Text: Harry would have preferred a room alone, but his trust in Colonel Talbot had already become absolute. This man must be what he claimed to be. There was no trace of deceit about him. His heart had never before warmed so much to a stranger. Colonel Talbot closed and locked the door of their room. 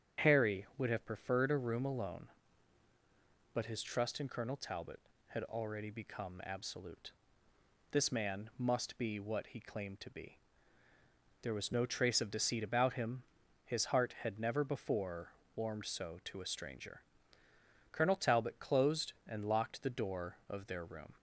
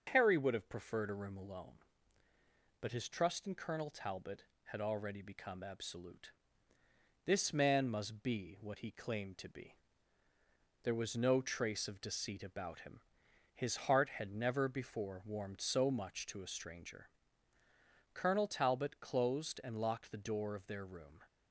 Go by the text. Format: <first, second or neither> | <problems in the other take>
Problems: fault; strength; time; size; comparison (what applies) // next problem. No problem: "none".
second | starts louder than the rest; strong; until 1.3 s; 8.5 dB; noticeable in the second // pauses between "before" and "warmed"; slight; at 15.2 s; 0.26 s long // skips "much"; at 16.2 s